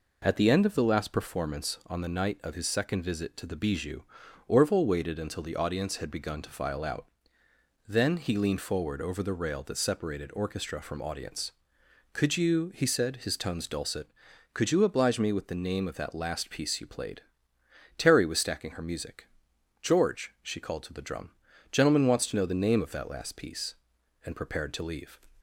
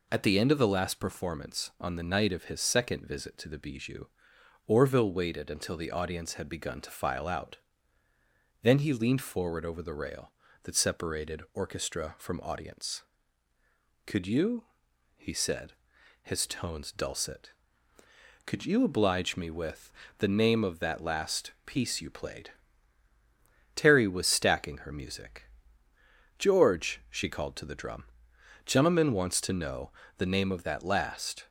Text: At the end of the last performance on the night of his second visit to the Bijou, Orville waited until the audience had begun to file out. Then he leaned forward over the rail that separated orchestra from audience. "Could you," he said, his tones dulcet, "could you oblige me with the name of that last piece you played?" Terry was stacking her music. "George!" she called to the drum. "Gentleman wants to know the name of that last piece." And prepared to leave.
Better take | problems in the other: first | pauses between "with" and "the"; slight; at 19.9 s; 0.26 s long // pauses between "know" and "the"; slight; at 29.9 s; 0.26 s long // stops before "piece And prepared to leave"; at 31.4 s

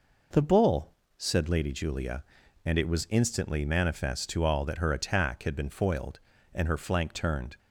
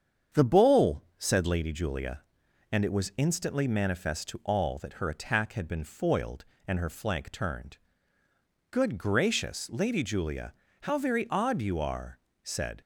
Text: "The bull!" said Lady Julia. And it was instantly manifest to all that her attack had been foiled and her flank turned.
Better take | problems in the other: first | starts louder than the rest; strong; until 1.4 s; 7.5 dB // goes on to say "Good gracious Lady Julia how very odd you are said"; strong; from 8.7 s on; 4.1 s long

